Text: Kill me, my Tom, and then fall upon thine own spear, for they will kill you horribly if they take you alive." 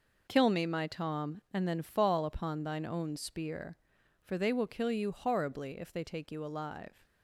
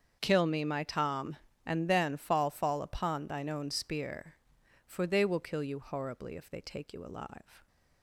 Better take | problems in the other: first | starts louder than the rest; strong; until 1.2 s; 7.5 dB // says "fall" twice; at 2.5 s

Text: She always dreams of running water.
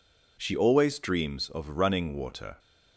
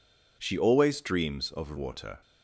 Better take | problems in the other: first | skips "running"; at 1.7 s

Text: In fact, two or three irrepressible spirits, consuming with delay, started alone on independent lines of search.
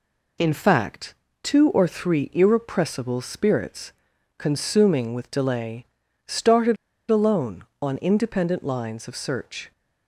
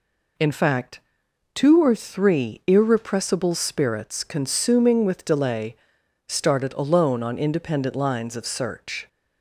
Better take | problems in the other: second | pauses between "started" and "alone"; slight; at 6.7 s; 0.33 s long

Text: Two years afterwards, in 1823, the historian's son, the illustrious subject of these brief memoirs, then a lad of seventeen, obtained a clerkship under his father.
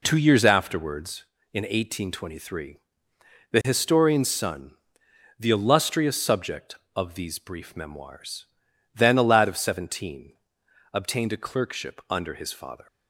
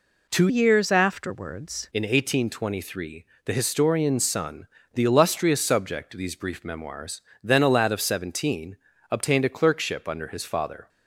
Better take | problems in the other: first | changes voice from "years" to "afterwards"; from 0.4 to 1.8 s; 1.4 s long

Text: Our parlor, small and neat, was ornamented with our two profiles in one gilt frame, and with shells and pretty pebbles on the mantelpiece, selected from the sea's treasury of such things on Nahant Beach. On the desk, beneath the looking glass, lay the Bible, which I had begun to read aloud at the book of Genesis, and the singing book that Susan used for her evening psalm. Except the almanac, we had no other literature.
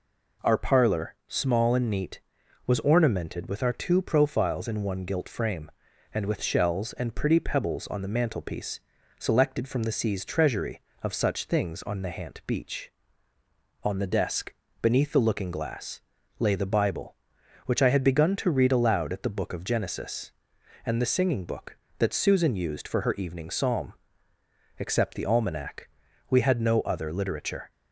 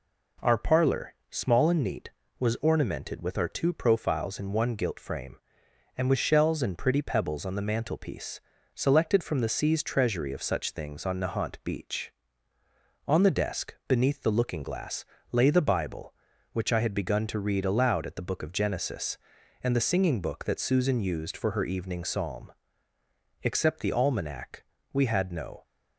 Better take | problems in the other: first | stops before "other literature"; at 25.6 s

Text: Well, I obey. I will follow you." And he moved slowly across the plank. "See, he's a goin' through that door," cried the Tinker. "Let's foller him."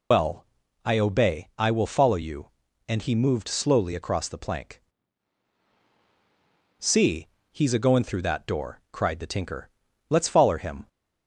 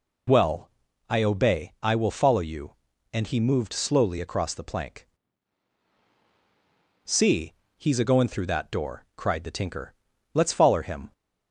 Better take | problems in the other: second | loses the start of "Well"; at 0.1 s; 75 ms

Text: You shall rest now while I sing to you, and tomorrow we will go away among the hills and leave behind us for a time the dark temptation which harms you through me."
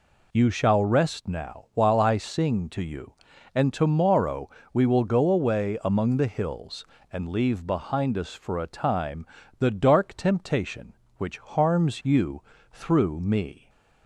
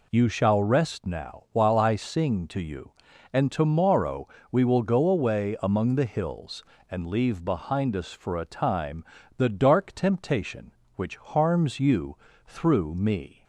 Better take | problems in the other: neither | pauses between "tomorrow" and "we"; slight; the same in both // pauses between "time" and "the"; slight; the same in both // pauses between "you" and "through"; slight; the same in both

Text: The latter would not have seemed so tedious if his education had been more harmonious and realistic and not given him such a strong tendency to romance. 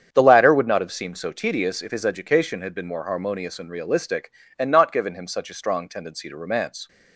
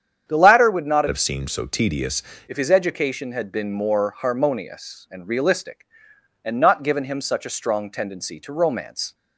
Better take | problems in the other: first | starts louder than the rest; strong; until 1.3 s; 8.5 dB; strong in the first // changes voice from "have" to "tedious"; from 1.0 to 2.2 s; 1.2 s long

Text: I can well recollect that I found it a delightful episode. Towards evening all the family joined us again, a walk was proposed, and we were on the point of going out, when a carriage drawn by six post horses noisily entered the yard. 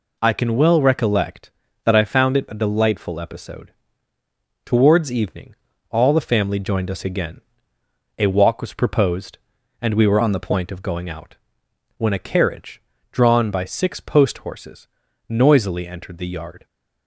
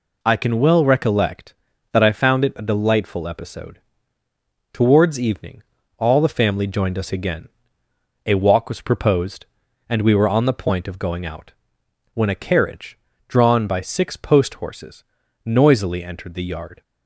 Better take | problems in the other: second | pauses between "evening" and "all"; at 5.5 s; 0.38 s long; also in the second // changes voice from "on" to "the"; from 10.2 to 10.3 s; 0.1 s long // pauses between "carriage" and "drawn"; slight; at 12.8 s; 0.30 s long; slight in the second // pauses between "horses" and "noisily"; at 14.8 s; 0.42 s long; also in the second

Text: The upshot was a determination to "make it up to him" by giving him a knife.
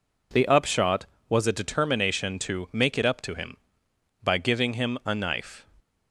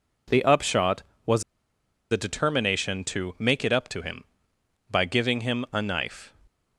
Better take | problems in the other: first | pauses between "was" and "a"; noticeable; at 1.4 s; 0.68 s long

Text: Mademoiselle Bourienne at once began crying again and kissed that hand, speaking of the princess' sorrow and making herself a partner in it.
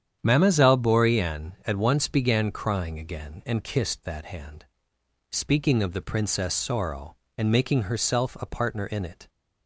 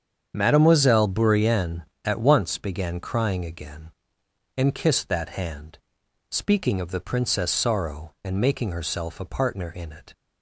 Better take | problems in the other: neither | starts louder than the rest; strong; the same in both

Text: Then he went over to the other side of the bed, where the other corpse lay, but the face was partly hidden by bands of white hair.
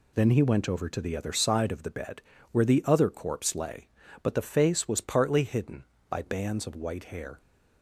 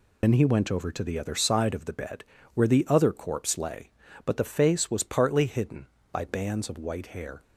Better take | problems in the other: first | loses the start of "Then"; at 0.2 s; 65 ms

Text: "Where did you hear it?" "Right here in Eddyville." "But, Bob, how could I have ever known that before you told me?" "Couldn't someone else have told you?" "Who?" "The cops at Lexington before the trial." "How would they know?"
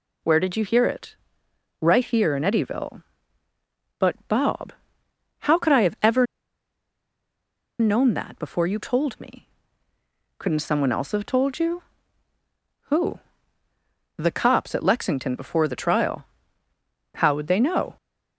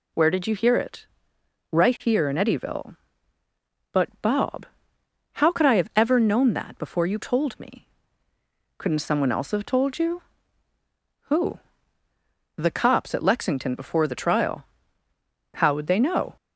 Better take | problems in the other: second | pauses between "ever" and "known"; strong; at 6.2 s; 1.5 s long

